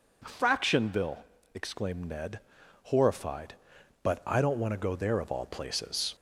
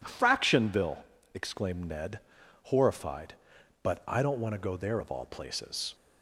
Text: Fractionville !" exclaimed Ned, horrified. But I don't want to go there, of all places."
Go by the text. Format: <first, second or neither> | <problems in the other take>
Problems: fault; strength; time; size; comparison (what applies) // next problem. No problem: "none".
second | gets louder; slight; throughout; 3 dB